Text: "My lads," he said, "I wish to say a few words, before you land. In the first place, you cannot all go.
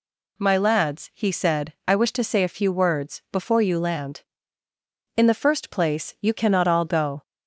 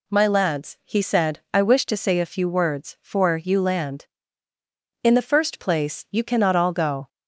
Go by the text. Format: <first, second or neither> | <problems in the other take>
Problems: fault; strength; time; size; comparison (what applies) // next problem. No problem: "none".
first | says "for" for "before"; at 2.9 s